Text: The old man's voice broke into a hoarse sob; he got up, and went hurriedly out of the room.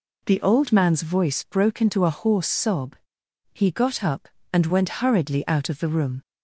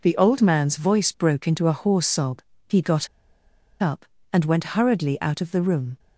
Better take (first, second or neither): first